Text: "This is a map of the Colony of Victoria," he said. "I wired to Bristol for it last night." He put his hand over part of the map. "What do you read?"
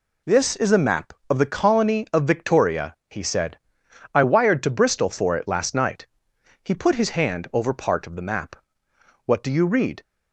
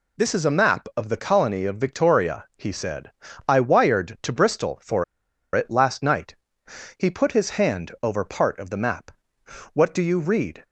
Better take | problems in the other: first | pauses between "for" and "it"; noticeable; at 5.0 s; 0.50 s long

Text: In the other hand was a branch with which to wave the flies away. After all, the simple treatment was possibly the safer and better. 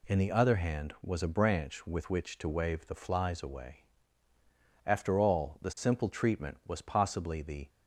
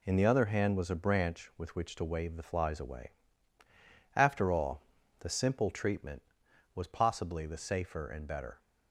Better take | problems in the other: second | stops before "safer and better"; at 7.6 s

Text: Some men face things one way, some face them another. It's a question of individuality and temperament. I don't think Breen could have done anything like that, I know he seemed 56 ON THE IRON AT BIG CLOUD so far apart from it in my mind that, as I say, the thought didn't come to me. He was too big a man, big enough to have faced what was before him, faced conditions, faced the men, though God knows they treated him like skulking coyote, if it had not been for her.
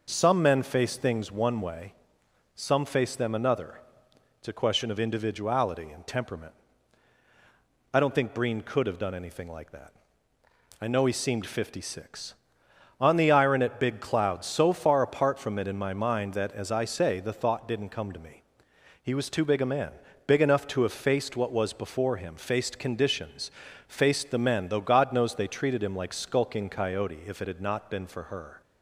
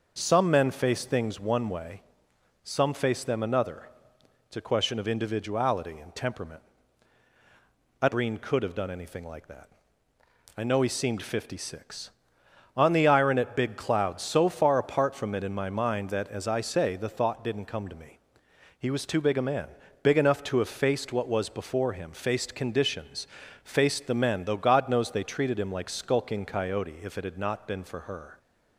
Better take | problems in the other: first | starts louder than the rest; noticeable; until 1.1 s; 6 dB // skips "don't think"; at 8.0 s

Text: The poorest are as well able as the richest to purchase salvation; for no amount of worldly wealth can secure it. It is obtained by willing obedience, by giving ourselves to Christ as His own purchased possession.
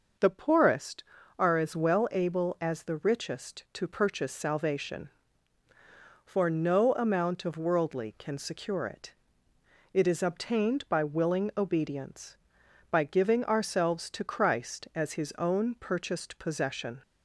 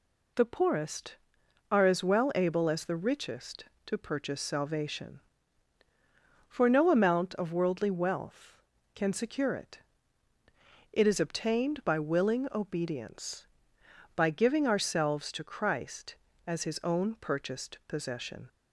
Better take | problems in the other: second | skips "wealth"; at 8.1 s

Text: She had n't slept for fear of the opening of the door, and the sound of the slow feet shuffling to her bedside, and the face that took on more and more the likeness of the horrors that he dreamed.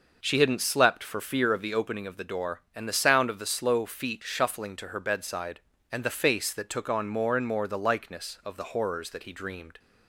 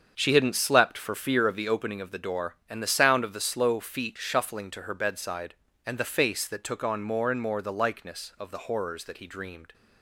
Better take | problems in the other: first | gets quieter; strong; throughout; 9.5 dB

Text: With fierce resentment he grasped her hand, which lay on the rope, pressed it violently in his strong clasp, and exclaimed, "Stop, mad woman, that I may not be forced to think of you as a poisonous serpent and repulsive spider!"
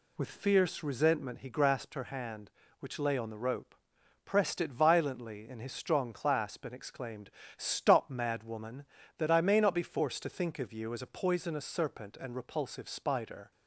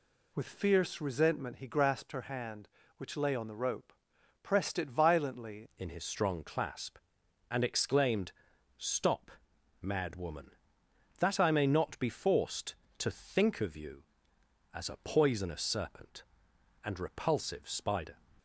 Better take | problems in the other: first | changes voice at "in"; from 5.7 s on; 12.4 s long

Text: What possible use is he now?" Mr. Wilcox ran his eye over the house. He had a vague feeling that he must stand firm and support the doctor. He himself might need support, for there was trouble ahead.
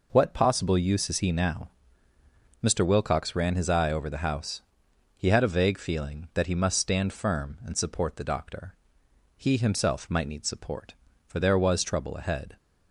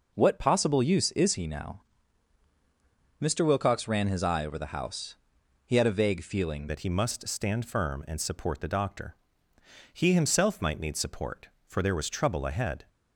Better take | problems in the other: first | changes voice at "that"; from 6.6 s on; 6.2 s long

